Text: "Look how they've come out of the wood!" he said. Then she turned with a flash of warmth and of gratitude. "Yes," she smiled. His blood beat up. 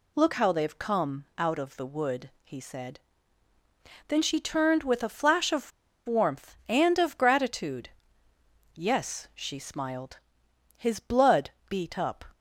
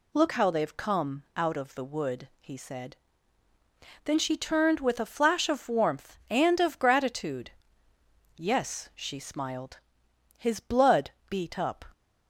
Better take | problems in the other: second | pauses between "of" and "warmth"; at 5.7 s; 0.36 s long // pauses between "blood" and "beat"; slight; at 11.5 s; 0.18 s long; slight in the second

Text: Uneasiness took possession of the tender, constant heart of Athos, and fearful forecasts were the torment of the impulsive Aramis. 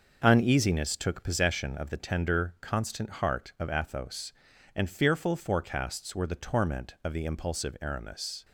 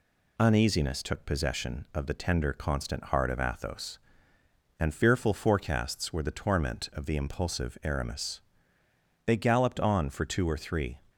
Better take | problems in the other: first | goes on to say "They galloped on for two or three"; strong; from 9.2 s on; 1.7 s long

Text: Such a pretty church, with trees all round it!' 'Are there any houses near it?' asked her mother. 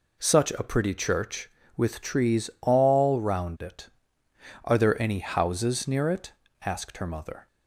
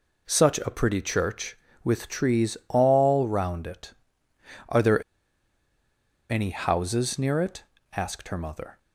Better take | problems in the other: first | pauses between "there" and "any"; strong; at 5.0 s; 1.2 s long

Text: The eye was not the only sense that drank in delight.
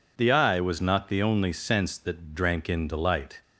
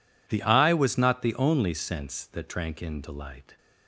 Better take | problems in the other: neither | none

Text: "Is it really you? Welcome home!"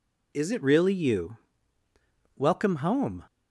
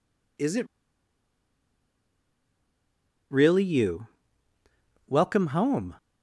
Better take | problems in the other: first | pauses between "it" and "really"; strong; at 0.6 s; 2.6 s long

